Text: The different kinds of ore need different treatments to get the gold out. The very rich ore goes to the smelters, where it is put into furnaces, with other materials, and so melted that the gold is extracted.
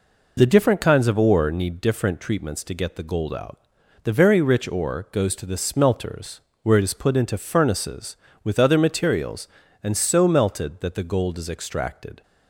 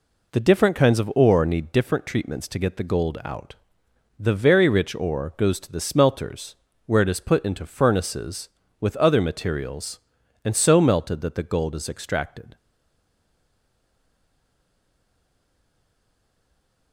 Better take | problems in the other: first | stays silent after the last word; strong; from 12.5 s on; 4.4 s long

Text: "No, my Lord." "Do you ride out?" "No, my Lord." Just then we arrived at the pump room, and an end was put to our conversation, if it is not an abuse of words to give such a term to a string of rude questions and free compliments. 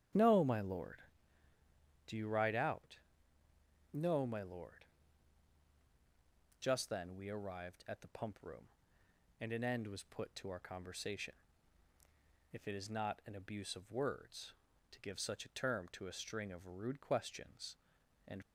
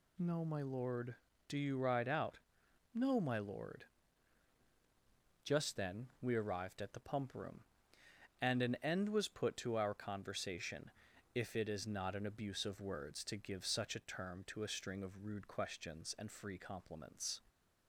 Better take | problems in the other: second | starts louder than the rest; strong; until 2.2 s; 10.5 dB // stops before "free compliments"; at 18.4 s

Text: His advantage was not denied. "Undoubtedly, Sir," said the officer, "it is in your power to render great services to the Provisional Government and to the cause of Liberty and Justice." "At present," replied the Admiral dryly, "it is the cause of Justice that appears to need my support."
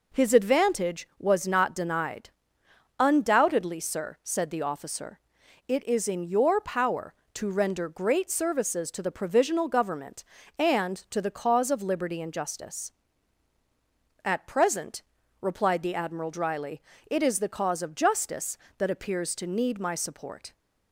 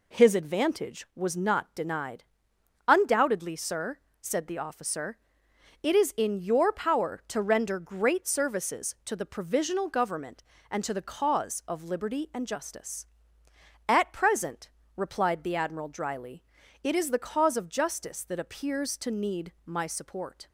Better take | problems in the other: neither | none

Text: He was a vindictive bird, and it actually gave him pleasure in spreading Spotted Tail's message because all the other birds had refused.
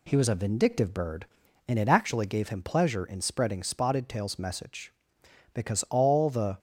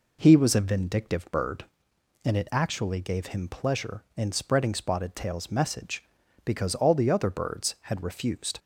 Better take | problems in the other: second | stops before "other birds had refused"; at 6.5 s

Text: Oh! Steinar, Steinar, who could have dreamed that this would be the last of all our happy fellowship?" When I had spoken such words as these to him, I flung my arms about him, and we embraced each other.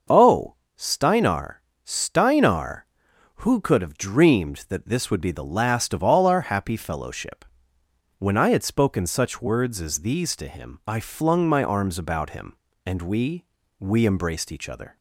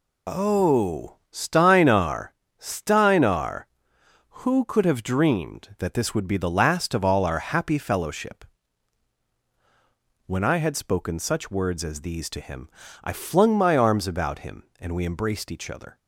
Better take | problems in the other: second | starts louder than the rest; until 1.3 s; 6.5 dB // says "we" twice; at 13.8 s

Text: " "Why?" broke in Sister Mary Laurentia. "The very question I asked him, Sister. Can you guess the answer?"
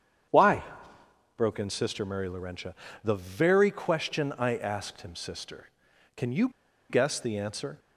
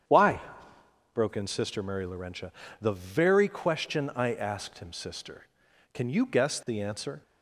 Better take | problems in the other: second | starts louder than the rest; strong; until 2.0 s; 8.5 dB; strong in the second // pauses between "you" and "guess"; at 6.4 s; 0.42 s long

